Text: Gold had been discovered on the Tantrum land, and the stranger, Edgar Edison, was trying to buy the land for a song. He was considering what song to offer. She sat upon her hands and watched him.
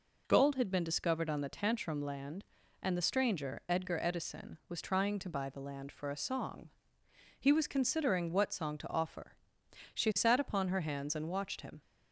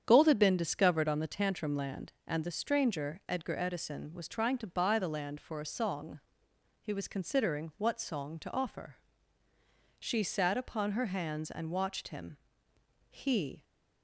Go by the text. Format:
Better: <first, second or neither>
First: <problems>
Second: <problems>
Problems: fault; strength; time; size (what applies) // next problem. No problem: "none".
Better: first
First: none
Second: starts louder than the rest; strong; until 1.0 s; 8.5 dB // goes on to say "He"; from 13.0 s on; 0.54 s long